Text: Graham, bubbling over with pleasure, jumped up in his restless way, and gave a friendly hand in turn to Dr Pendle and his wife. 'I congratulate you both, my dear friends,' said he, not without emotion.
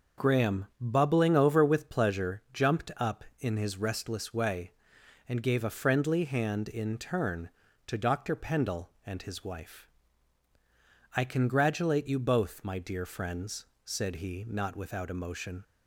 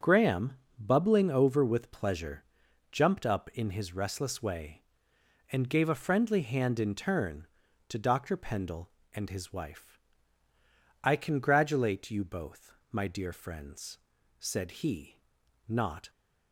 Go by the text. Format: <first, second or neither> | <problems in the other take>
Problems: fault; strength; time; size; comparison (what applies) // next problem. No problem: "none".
first | starts louder than the rest; until 1.2 s; 6.5 dB // stops before "without emotion"; at 16.0 s